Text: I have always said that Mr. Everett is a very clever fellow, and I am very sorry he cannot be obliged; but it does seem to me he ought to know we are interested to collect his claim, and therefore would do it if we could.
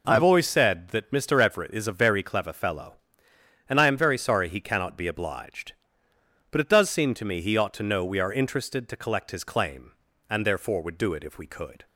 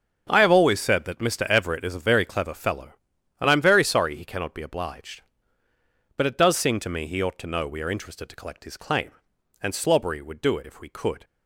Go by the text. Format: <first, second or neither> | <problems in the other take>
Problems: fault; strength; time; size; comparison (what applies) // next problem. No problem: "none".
first | starts louder than the rest; strong; until 1.3 s; 7 dB // says "slobbery" for "therefore"; at 9.7 s